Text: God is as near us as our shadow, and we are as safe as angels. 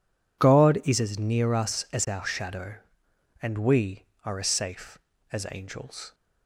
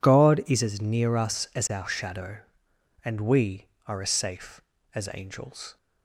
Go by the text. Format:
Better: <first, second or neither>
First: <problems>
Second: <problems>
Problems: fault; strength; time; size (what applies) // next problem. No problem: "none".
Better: neither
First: none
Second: none